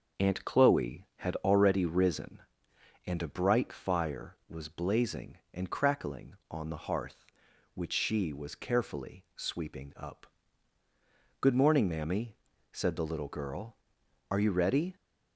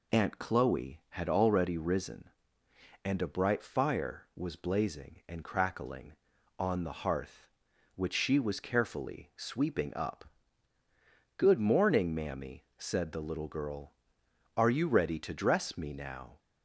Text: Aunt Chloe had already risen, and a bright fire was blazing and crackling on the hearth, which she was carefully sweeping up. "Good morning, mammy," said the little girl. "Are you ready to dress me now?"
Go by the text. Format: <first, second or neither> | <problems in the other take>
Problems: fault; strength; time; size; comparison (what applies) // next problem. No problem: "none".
second | starts louder than the rest; noticeable; until 1.2 s; 6 dB // stops before "to dress me now"; at 14.9 s